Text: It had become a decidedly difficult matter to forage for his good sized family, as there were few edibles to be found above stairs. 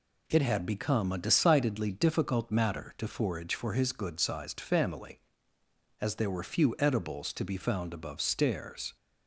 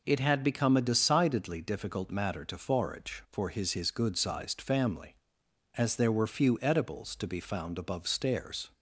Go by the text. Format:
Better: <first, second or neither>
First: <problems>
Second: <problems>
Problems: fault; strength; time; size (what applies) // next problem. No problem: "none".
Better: first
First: none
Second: says "his" twice; at 3.7 s